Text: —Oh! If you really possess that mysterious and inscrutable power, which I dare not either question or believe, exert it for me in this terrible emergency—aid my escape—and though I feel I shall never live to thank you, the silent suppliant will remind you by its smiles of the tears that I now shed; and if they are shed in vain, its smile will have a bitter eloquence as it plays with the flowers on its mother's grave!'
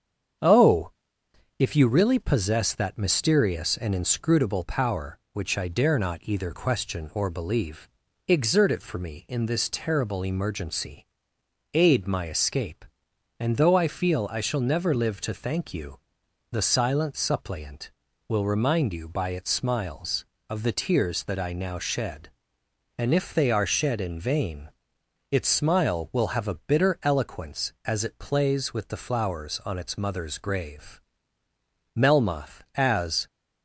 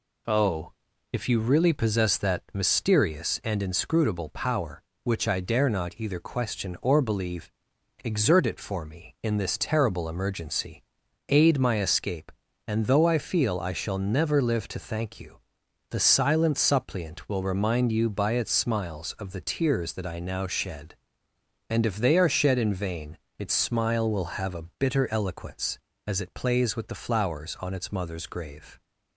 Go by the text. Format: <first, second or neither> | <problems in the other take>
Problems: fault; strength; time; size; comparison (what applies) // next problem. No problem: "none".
second | starts louder than the rest; strong; until 2.0 s; 7.5 dB // goes on to say "Melmoth as"; from 31.9 s on; 1.3 s long